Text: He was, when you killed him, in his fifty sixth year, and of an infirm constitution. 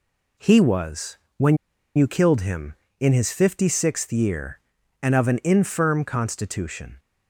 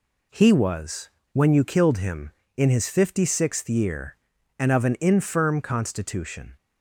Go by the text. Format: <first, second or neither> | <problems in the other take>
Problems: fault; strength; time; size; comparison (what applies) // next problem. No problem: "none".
second | pauses between "when" and "you"; at 1.5 s; 0.40 s long